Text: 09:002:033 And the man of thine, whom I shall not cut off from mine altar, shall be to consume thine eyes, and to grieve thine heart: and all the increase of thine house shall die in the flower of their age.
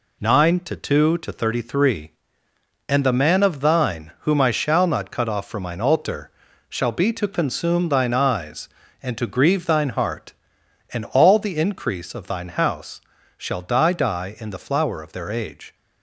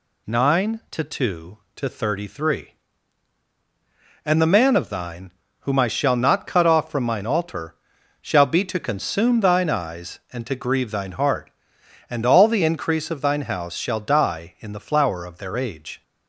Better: second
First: pauses between "house" and "shall"; slight; at 13.0 s; 0.34 s long // says "die" twice; at 13.9 s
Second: none

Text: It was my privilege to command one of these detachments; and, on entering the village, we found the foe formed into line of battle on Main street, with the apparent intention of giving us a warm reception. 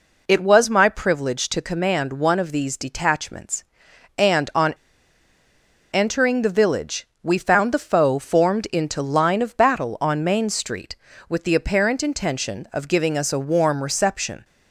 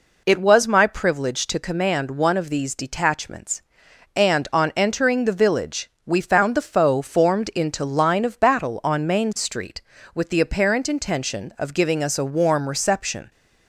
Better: second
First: pauses between "on" and "entering"; at 4.7 s; 1.1 s long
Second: none

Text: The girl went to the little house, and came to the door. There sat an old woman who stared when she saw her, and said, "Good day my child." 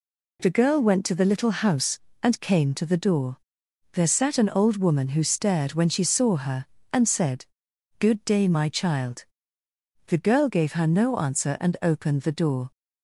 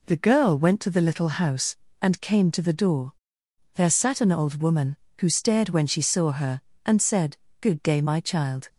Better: second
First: goes on to say "The girl gave her no answer and opened the door"; strong; from 10.0 s on; 2.6 s long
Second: none

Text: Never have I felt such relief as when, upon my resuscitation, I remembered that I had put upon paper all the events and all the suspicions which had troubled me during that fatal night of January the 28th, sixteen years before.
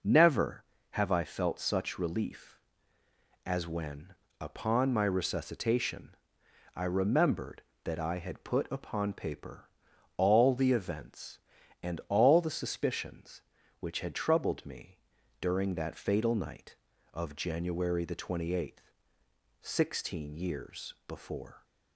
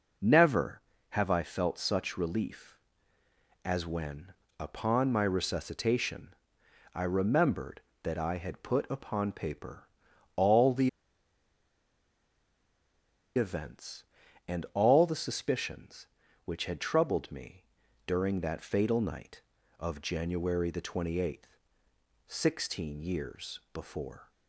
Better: first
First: pauses between "paper" and "all"; noticeable; at 9.6 s; 0.48 s long // pauses between "me" and "during"; at 14.9 s; 0.44 s long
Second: pauses between "paper" and "all"; noticeable; at 9.8 s; 0.48 s long // pauses between "the" and "events"; strong; at 10.8 s; 2.4 s long // pauses between "me" and "during"; at 17.6 s; 0.44 s long

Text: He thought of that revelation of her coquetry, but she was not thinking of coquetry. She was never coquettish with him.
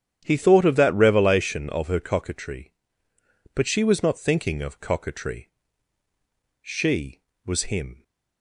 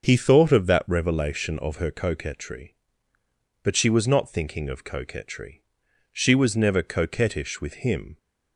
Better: second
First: starts louder than the rest; strong; until 1.2 s; 9.5 dB // skips "never coquettish with"; at 7.6 s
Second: starts louder than the rest; until 1.0 s; 6.5 dB

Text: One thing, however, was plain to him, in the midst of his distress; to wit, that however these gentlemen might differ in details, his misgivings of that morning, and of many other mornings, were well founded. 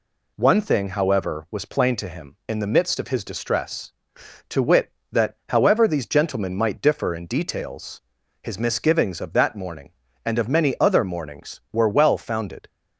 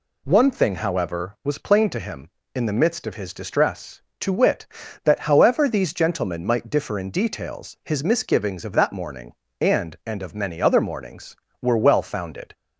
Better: first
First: none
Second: says "and" twice; at 10.0 s

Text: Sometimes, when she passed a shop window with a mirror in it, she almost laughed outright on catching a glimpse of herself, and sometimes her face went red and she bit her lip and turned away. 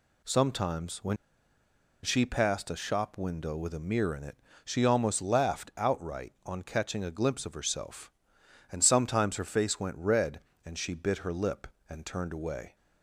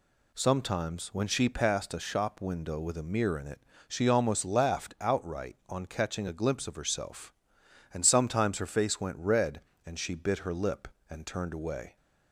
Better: second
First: pauses between "when" and "she"; noticeable; at 1.1 s; 0.86 s long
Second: none

